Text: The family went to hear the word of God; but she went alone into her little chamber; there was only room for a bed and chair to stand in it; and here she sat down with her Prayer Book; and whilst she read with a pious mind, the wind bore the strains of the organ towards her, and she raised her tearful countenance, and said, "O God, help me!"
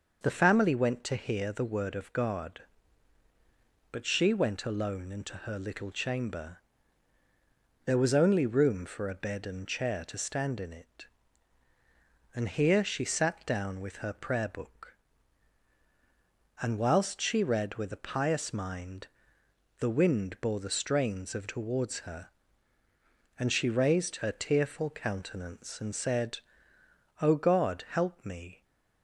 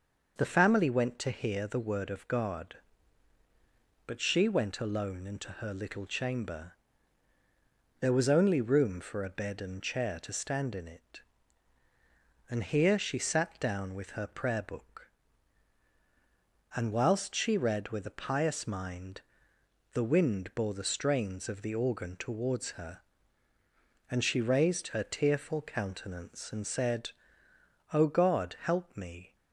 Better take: second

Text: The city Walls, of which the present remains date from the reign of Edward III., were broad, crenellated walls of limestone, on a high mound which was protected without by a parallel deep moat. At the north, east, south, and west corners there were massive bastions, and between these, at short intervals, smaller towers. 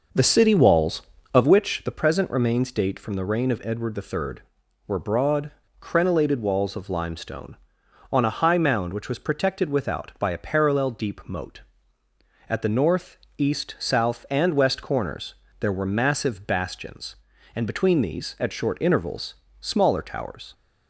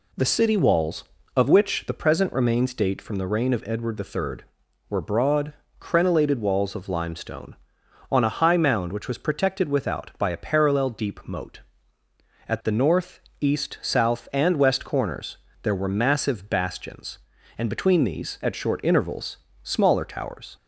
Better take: second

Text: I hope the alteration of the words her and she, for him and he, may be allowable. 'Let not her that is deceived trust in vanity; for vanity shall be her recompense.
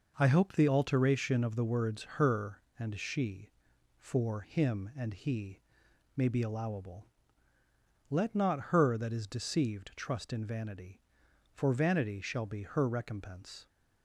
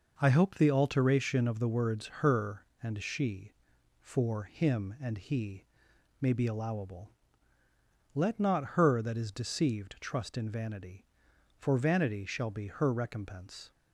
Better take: neither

